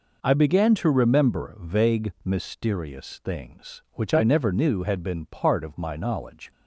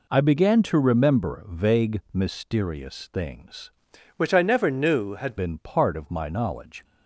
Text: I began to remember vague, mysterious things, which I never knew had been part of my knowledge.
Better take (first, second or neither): first